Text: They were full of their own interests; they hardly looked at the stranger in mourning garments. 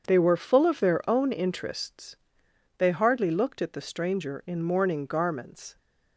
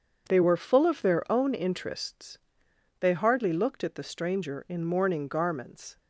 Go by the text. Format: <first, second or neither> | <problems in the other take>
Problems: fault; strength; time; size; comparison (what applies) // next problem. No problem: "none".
neither | none